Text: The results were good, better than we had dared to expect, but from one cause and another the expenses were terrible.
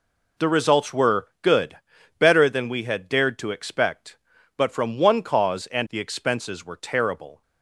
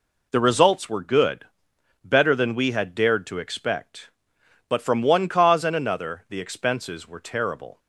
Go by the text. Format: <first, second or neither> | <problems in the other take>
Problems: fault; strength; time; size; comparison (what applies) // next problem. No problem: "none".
second | skips "another"; at 5.8 s